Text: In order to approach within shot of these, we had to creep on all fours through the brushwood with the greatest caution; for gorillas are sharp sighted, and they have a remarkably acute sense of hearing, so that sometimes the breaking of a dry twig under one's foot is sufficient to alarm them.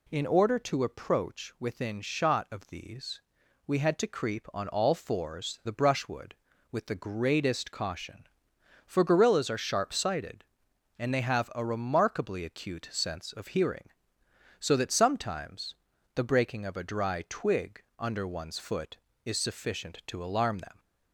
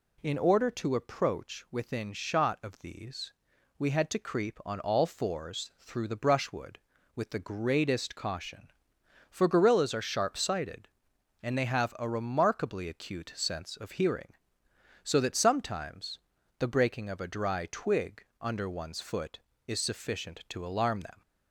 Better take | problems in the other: second | skips "through"; at 5.6 s // pauses between "sometimes" and "the"; at 15.7 s; 0.40 s long; also in the second // pauses between "twig" and "under"; slight; at 17.8 s; 0.16 s long; slight in the second

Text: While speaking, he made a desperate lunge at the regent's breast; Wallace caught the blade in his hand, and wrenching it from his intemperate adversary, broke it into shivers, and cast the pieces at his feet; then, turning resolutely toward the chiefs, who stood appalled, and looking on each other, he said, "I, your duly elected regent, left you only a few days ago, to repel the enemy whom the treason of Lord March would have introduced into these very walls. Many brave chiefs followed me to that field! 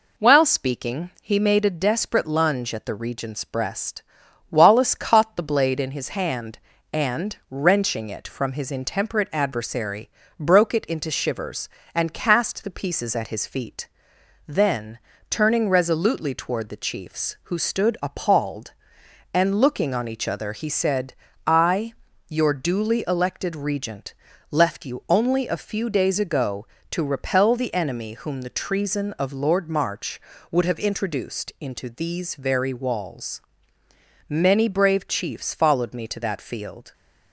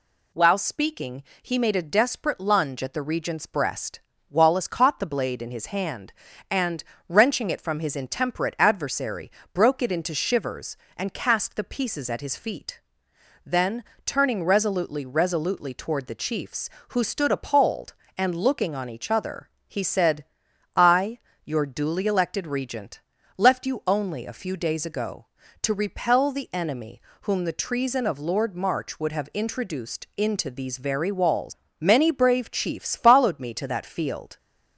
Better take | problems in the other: first | pauses between "and" and "wrenching"; slight; at 6.8 s; 0.24 s long // says "resolutely" twice; at 15.0 s // pauses between "enemy" and "whom"; slight; at 27.0 s; 0.20 s long

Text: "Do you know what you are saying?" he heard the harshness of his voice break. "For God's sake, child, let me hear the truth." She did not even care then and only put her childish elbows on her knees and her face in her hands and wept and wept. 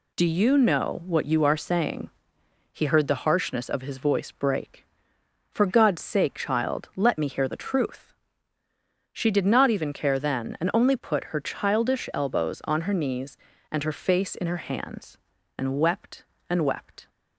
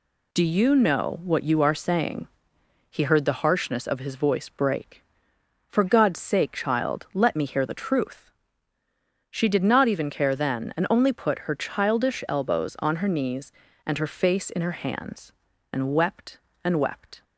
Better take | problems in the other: neither | none

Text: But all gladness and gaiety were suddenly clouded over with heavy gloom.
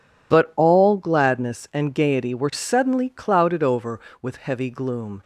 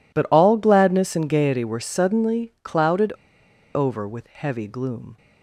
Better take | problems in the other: first | pauses between "clouded" and "over"; noticeable; at 3.1 s; 0.62 s long

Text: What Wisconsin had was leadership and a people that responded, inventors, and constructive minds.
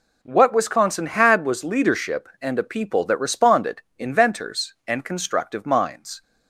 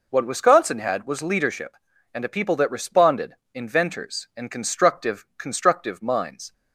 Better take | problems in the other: first | says "constructive" twice; at 5.3 s

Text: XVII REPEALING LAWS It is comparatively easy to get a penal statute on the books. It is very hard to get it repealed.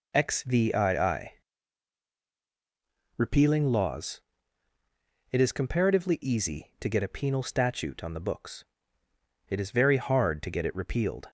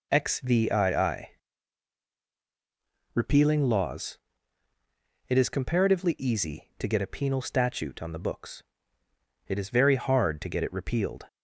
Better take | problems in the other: neither | pauses between "XVII" and "REPEALING"; strong; the same in both // pauses between "LAWS" and "It"; the same in both

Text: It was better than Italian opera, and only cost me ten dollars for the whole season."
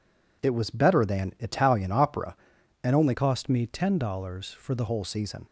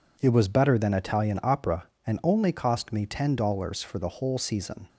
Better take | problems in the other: second | changes voice from "cost" to "the"; from 3.1 to 4.8 s; 1.7 s long

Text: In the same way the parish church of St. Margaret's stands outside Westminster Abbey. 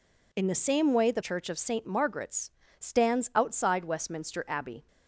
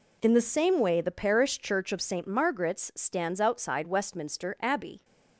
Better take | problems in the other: second | skips "parish"; at 1.2 s // pauses between "Margaret's" and "stands"; slight; at 2.4 s; 0.30 s long

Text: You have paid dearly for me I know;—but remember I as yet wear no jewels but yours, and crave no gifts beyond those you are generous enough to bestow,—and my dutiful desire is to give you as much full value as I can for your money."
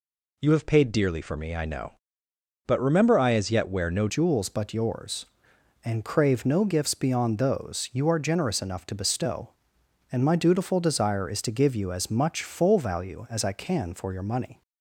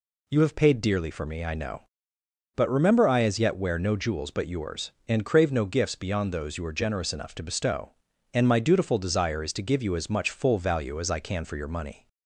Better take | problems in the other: second | changes voice at "jewels"; from 4.0 s on; 10.6 s long

